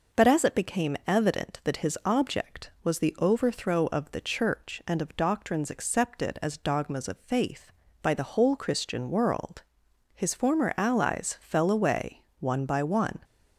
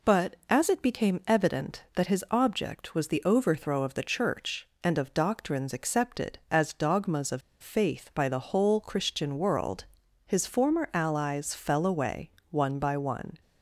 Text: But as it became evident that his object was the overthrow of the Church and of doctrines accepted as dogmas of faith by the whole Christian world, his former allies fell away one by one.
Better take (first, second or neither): first